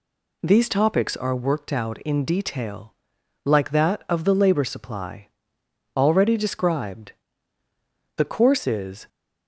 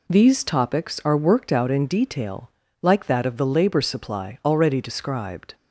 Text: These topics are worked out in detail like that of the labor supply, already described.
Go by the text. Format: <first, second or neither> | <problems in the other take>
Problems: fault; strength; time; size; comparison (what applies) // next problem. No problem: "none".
second | pauses between "detail" and "like"; noticeable; at 2.9 s; 0.50 s long; slight in the second // goes on to say "The course is"; noticeable; from 8.1 s on; 0.90 s long